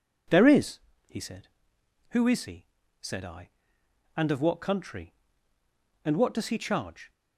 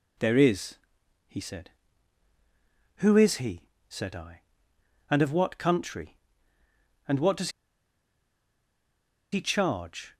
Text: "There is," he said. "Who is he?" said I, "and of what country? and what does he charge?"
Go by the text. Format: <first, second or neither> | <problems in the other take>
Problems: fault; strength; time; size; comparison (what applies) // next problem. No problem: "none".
first | pauses between "does" and "he"; strong; at 7.4 s; 1.8 s long